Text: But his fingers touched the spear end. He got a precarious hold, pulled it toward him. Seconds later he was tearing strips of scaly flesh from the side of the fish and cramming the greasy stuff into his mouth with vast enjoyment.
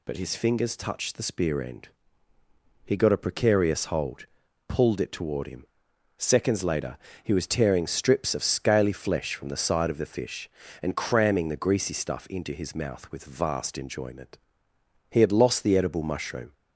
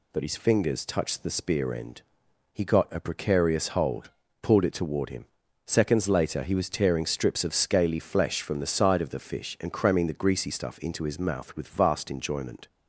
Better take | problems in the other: second | pauses between "later" and "he"; slight; at 6.9 s; 0.26 s long // goes on to say "He had lost the edible mushroom"; from 15.0 s on; 1.4 s long

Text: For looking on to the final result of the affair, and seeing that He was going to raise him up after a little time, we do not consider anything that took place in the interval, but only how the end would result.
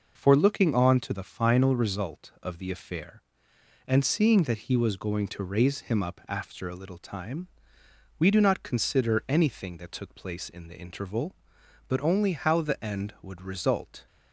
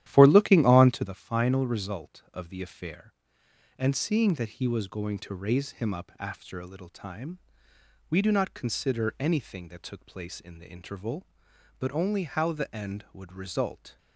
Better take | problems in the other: first | starts louder than the rest; strong; until 1.1 s; 12.5 dB

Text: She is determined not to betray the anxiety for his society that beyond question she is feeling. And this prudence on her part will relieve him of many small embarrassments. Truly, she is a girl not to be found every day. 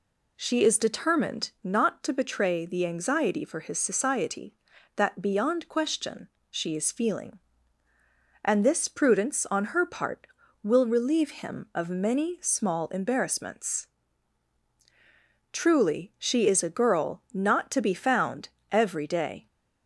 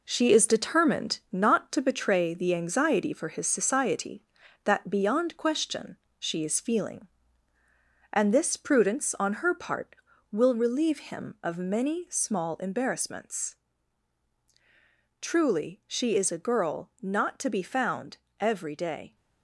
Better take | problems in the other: first | gets quieter; noticeable; throughout; 6 dB // pauses between "question" and "she"; slight; at 5.9 s; 0.22 s long; slight in the first // pauses between "found" and "every"; slight; at 18.1 s; 0.24 s long; slight in the first

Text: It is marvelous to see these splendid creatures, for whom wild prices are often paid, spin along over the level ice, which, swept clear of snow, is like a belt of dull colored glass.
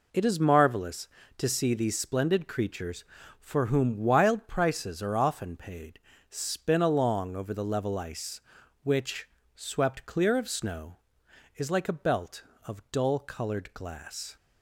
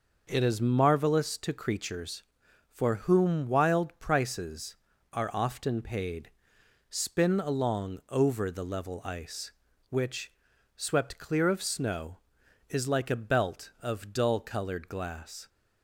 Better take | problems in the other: first | skips "see these splendid"; at 1.5 s

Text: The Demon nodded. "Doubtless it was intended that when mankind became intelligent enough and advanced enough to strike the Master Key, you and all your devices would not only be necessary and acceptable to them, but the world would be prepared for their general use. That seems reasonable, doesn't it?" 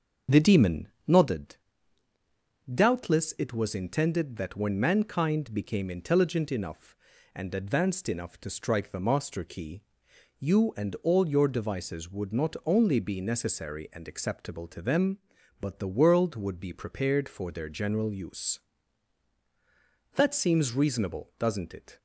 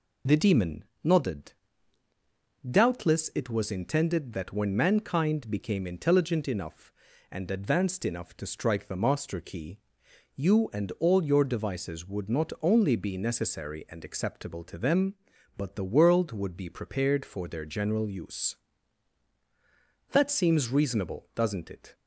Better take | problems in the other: second | starts louder than the rest; until 1.5 s; 6.5 dB // pauses between "Demon" and "nodded"; slight; at 0.8 s; 0.22 s long; slight in the second

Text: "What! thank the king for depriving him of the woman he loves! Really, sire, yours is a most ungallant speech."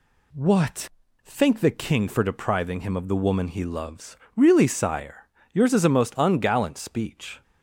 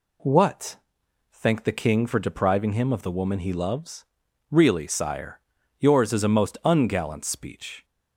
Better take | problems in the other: neither | none

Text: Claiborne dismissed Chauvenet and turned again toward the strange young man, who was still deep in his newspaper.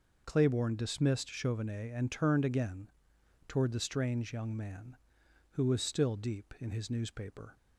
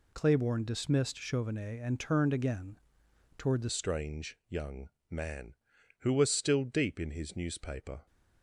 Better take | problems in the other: first | pauses between "again" and "toward"; noticeable; at 2.7 s; 0.58 s long; noticeable in the first // changes voice at "strange"; from 3.6 s on; 4.4 s long // pauses between "young" and "man"; slight; at 4.8 s; 0.20 s long

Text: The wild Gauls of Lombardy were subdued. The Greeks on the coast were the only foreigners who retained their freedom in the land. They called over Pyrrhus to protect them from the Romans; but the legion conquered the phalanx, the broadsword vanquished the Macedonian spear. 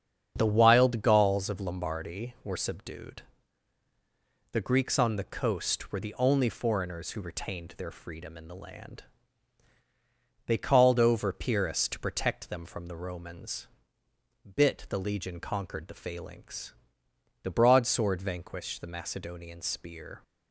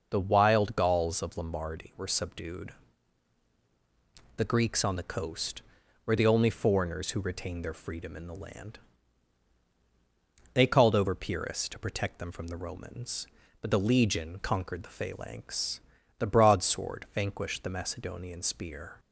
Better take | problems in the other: second | starts louder than the rest; strong; until 1.3 s; 7.5 dB // says "bit" for "but"; at 14.5 s

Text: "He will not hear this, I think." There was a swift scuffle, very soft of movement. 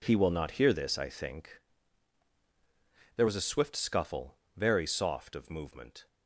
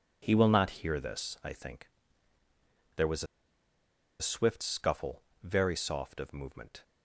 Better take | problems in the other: first | pauses between "was" and "a"; noticeable; at 3.2 s; 0.96 s long

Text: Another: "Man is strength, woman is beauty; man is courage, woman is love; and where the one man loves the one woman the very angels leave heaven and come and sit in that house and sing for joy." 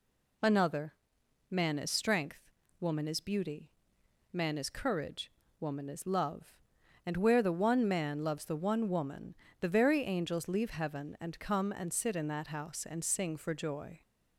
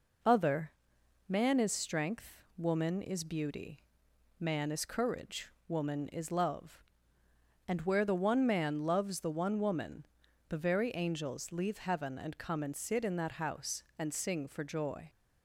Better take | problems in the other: first | says "Other" for "Another"; at 0.2 s // pauses between "woman" and "the"; at 10.0 s; 0.44 s long; slight in the first

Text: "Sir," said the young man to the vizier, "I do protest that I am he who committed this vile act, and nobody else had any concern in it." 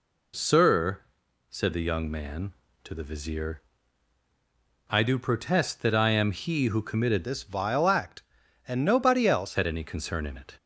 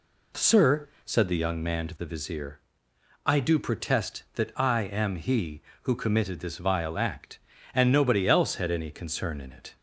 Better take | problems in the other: second | changes voice from "this" to "else"; from 7.2 to 9.5 s; 2.3 s long

